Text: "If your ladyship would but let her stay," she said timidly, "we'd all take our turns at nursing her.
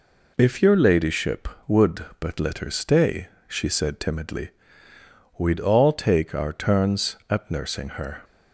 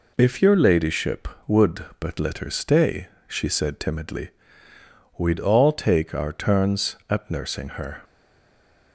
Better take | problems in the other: first | stays silent after the last word; slight; from 8.0 s on; 0.9 s long

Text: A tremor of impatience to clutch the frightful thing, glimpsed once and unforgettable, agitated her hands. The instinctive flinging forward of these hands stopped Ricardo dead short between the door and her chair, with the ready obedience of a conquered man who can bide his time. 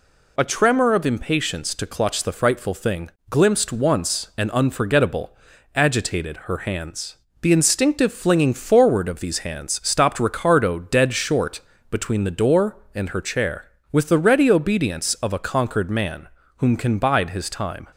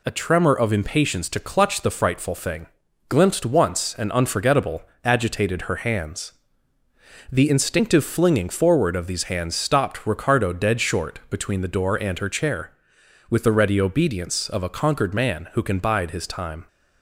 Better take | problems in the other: second | pauses between "short" and "between"; slight; at 11.5 s; 0.30 s long // says "whom" for "who"; at 16.5 s

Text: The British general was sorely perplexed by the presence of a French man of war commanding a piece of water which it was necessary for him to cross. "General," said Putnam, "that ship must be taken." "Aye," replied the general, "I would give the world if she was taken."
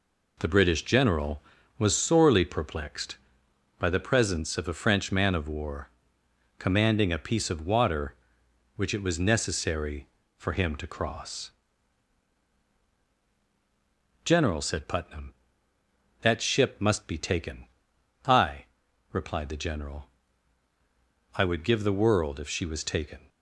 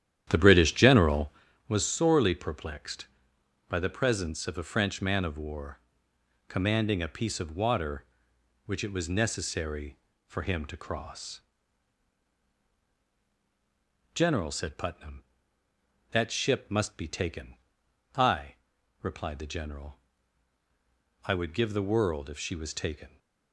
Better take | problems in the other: first | starts louder than the rest; strong; until 1.4 s; 10.5 dB // pauses between "war" and "commanding"; noticeable; at 5.7 s; 0.70 s long; noticeable in the first

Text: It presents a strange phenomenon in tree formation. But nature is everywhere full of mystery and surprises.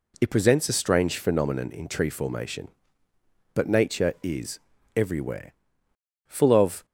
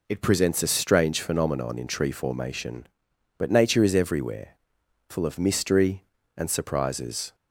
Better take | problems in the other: second | pauses between "is" and "everywhere"; slight; at 4.5 s; 0.36 s long // pauses between "everywhere" and "full"; noticeable; at 5.5 s; 0.74 s long; noticeable in the second // stops before "mystery and surprises"; at 6.8 s

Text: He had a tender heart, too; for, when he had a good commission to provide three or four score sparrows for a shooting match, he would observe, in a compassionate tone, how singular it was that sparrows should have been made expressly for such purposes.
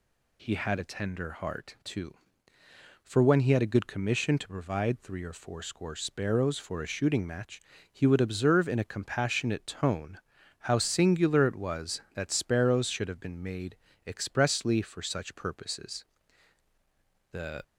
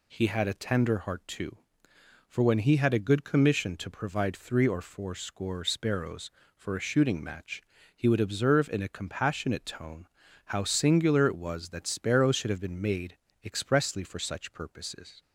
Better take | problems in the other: second | pauses between "made" and "expressly"; slight; at 13.7 s; 0.32 s long; slight in the second // goes on to say "The"; slight; from 17.3 s on; 0.30 s long

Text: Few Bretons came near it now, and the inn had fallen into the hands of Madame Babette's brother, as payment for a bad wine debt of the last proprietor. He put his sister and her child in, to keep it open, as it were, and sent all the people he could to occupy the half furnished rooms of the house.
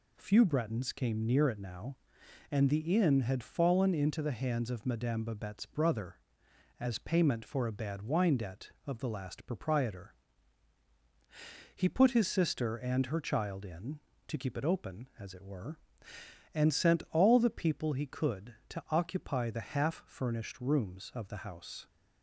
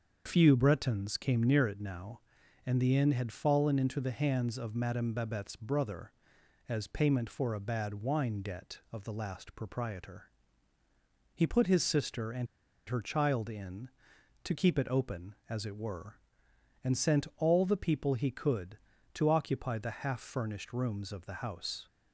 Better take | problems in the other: first | starts louder than the rest; until 1.2 s; 6.5 dB // pauses between "and" and "her"; at 12.4 s; 0.41 s long

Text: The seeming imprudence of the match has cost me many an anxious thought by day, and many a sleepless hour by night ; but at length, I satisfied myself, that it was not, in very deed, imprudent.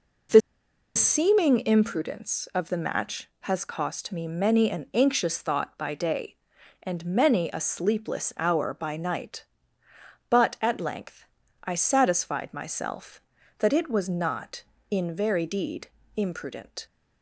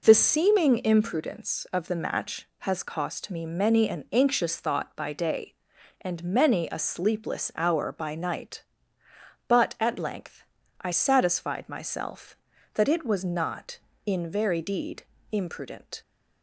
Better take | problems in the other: second | pauses between "The" and "seeming"; noticeable; at 0.4 s; 0.55 s long

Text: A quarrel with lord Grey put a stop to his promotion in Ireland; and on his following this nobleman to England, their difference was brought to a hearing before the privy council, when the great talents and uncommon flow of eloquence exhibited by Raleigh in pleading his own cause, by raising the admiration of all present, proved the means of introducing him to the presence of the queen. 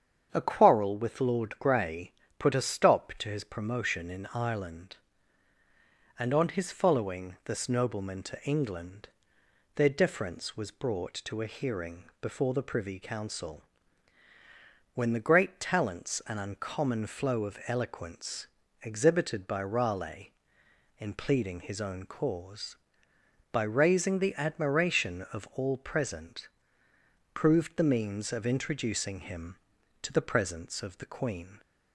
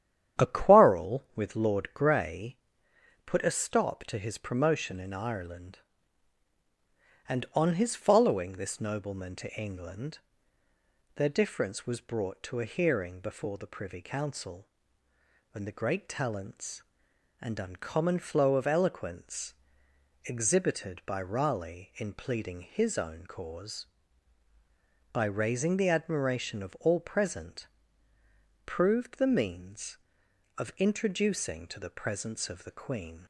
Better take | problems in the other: first | starts louder than the rest; strong; until 1.4 s; 10 dB; strong in the first // pauses between "Grey" and "put"; noticeable; at 2.5 s; 0.68 s long; slight in the first // pauses between "eloquence" and "exhibited"; noticeable; at 19.5 s; 0.72 s long; slight in the first // skips "him"; at 31.6 s

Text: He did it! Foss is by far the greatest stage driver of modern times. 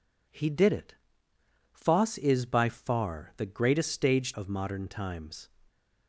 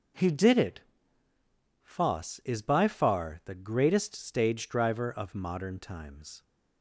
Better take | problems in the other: second | skips "driver"; at 4.3 s

